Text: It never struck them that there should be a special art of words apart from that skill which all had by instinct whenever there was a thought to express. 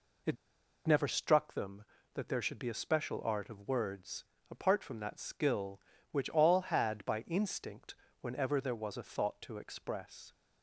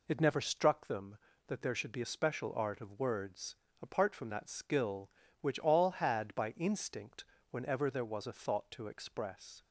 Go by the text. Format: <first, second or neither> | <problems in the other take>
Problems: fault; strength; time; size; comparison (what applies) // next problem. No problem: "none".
second | pauses between "It" and "never"; noticeable; at 0.3 s; 0.52 s long // pauses between "words" and "apart"; slight; at 4.2 s; 0.26 s long; slight in the second // pauses between "instinct" and "whenever"; slight; at 7.9 s; 0.26 s long; slight in the second